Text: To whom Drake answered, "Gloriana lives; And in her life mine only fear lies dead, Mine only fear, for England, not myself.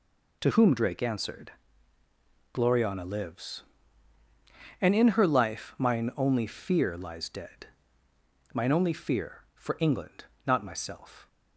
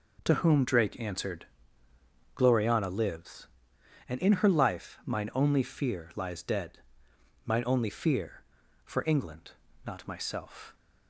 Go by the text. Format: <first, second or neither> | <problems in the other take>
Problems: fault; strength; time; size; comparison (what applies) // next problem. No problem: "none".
neither | none